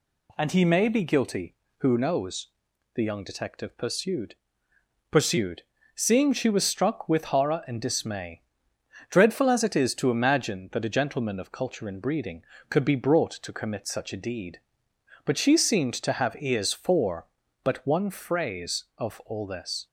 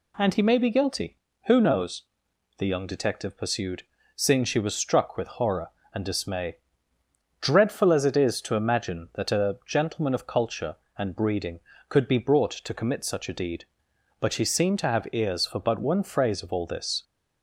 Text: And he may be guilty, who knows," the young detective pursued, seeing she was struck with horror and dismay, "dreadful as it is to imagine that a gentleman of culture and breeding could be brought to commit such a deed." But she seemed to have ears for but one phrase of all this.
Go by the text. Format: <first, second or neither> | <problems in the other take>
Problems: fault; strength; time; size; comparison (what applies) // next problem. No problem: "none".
second | says "pursued" twice; at 5.1 s